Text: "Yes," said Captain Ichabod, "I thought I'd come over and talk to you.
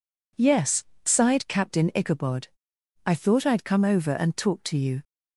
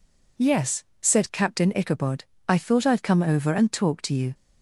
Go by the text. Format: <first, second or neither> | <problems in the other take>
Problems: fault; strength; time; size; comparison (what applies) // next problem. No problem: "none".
second | says "sighed" for "said"; at 1.0 s